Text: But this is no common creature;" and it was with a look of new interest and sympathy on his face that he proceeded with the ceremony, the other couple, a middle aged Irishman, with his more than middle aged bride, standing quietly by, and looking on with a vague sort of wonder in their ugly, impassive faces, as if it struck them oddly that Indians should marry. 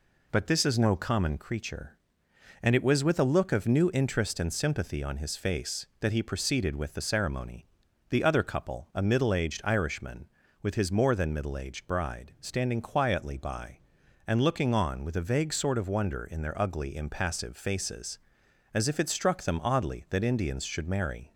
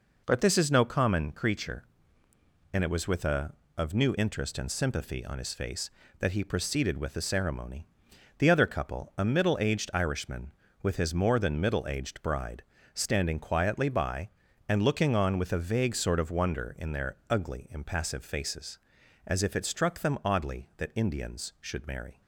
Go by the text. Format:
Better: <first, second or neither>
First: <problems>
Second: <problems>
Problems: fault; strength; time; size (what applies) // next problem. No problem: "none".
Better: first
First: none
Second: skips "look"; at 3.6 s